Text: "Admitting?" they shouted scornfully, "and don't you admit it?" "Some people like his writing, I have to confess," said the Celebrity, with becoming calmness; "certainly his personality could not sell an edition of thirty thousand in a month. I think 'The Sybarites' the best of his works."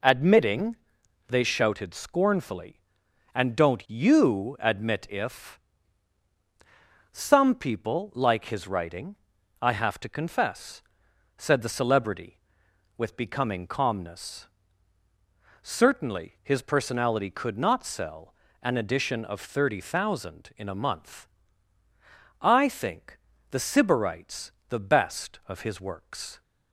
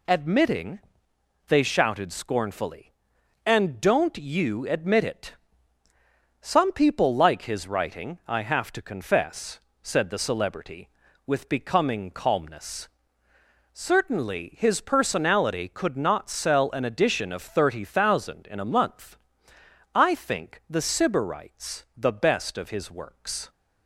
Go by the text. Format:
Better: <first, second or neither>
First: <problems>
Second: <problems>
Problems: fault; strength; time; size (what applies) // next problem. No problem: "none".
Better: second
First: says "if" for "it"; at 5.0 s // pauses between "sell" and "an"; slight; at 18.3 s; 0.28 s long // pauses between "think" and "The"; slight; at 23.1 s; 0.34 s long // pauses between "Sybarites" and "the"; slight; at 24.5 s; 0.16 s long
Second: none